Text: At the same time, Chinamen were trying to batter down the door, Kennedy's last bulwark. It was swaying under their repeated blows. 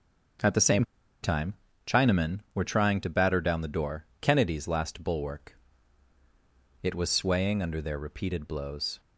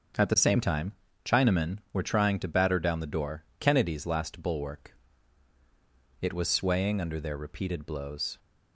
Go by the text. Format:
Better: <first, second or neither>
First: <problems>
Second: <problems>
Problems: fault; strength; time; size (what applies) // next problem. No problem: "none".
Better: second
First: starts louder than the rest; until 2.1 s; 7 dB // pauses between "same" and "time"; at 0.8 s; 0.38 s long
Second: starts louder than the rest; until 1.5 s; 7 dB